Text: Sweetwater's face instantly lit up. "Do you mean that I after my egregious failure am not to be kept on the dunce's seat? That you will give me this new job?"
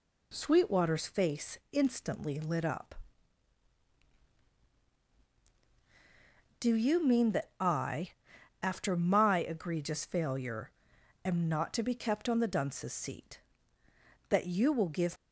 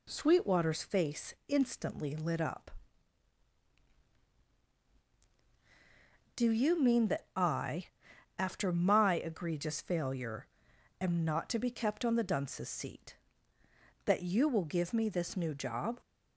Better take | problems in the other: second | pauses between "I" and "after"; noticeable; at 8.1 s; 0.50 s long; noticeable in the second // pauses between "failure" and "am"; noticeable; at 10.7 s; 0.52 s long; noticeable in the second // stops before "me this new job"; at 15.1 s

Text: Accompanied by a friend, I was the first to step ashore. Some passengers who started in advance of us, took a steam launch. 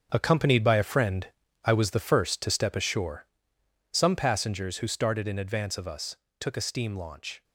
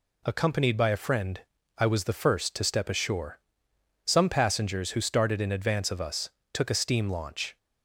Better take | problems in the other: second | gets quieter; strong; throughout; 10.5 dB

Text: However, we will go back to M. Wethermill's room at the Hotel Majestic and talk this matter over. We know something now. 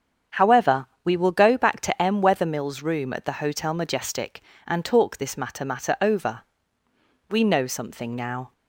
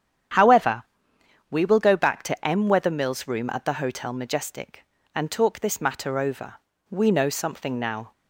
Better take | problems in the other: second | starts louder than the rest; strong; until 1.5 s; 8 dB; strong in the second // says "matter" twice; at 5.6 s

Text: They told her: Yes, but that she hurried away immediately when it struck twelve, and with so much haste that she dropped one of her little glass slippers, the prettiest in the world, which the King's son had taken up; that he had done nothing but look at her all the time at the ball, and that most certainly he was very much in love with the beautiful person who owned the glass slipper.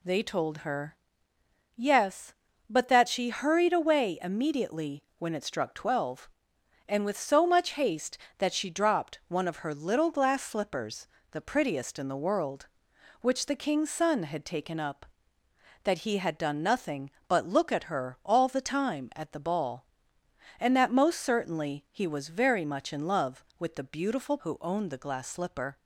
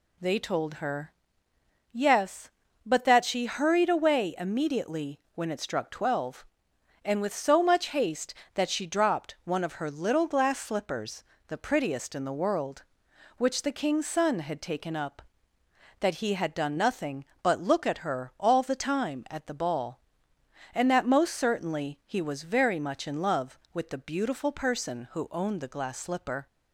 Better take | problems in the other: second | skips "person"; at 24.3 s

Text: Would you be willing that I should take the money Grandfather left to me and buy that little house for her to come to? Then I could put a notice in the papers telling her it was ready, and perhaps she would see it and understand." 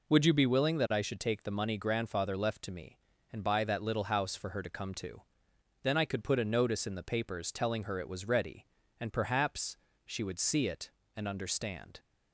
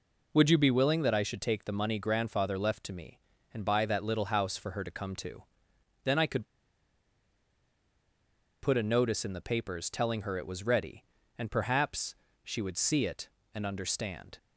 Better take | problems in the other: first | pauses between "could" and "put"; strong; at 6.4 s; 2.1 s long // pauses between "perhaps" and "she"; slight; at 12.1 s; 0.30 s long; slight in the first

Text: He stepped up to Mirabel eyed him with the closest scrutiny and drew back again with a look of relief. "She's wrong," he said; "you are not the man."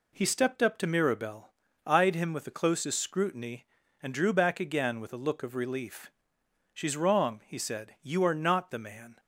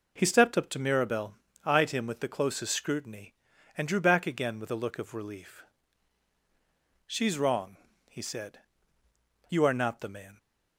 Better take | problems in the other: neither | pauses between "Mirabel" and "eyed"; slight; the same in both

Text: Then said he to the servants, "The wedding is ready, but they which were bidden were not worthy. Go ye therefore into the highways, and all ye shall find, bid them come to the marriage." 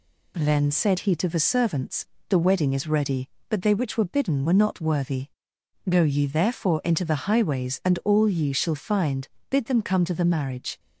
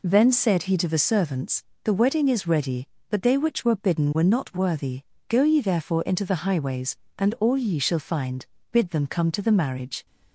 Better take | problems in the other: neither | none

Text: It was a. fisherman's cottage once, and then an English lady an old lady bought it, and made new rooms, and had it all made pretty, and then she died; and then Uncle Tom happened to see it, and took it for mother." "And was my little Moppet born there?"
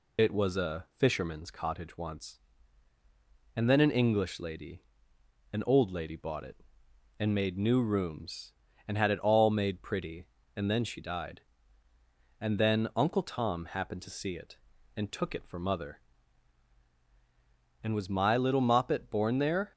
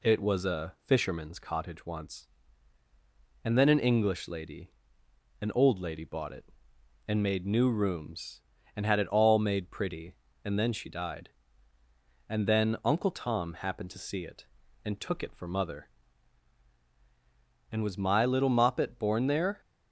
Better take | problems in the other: second | loses the start of "It"; at 0.1 s; 50 ms // pauses between "lady" and "an"; noticeable; at 4.8 s; 0.70 s long; noticeable in the second

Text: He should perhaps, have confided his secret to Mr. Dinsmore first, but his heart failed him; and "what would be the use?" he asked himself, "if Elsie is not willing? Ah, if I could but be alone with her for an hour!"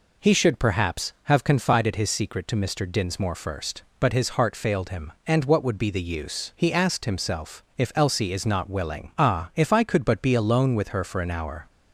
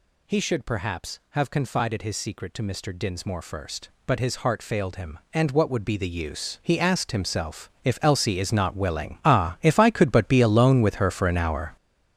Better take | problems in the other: first | gets louder; strong; throughout; 10.5 dB

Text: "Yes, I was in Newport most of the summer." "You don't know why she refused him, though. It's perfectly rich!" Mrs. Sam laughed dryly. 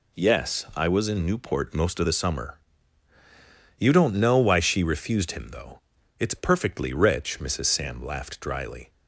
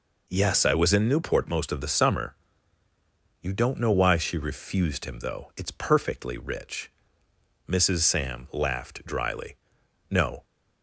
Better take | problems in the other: first | goes on to say "No"; slight; from 10.0 s on; 0.36 s long

